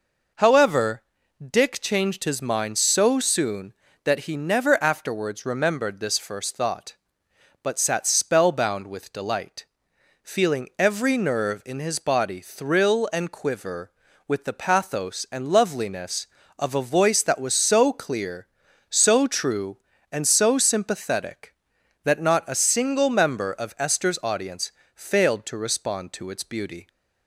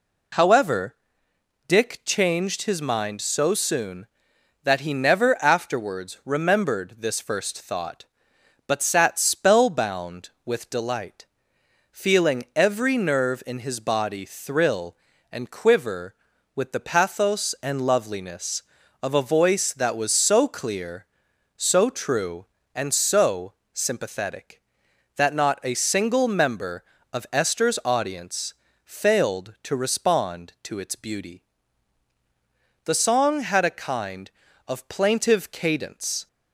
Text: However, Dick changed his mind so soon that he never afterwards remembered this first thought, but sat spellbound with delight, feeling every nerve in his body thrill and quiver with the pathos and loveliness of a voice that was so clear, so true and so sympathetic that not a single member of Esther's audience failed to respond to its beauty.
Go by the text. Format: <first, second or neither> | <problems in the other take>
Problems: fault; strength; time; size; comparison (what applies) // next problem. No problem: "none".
first | pauses between "so" and "sympathetic"; slight; at 23.5 s; 0.18 s long // pauses between "audience" and "failed"; slight; at 28.5 s; 0.28 s long; slight in the first // goes on to say "The song had a kind of plaintive cadence"; strong; from 32.8 s on; 3.4 s long